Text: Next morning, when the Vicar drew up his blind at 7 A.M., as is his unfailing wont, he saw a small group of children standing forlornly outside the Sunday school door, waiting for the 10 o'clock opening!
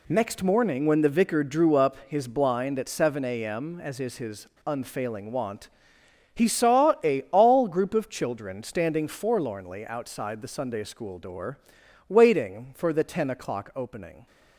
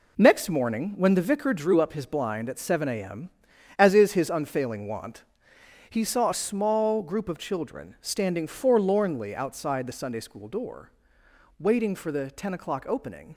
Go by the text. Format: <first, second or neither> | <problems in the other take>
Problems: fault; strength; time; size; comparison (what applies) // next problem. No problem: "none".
second | pauses between "his" and "unfailing"; slight; at 4.4 s; 0.19 s long // says "all" for "small"; at 7.2 s